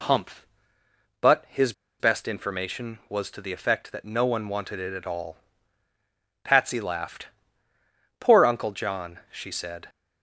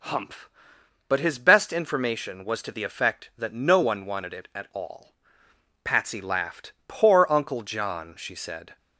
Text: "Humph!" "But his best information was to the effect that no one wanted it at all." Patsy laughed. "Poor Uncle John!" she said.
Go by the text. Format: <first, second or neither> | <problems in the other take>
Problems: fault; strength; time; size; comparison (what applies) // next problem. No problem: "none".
second | pauses between "his" and "best"; slight; at 1.7 s; 0.28 s long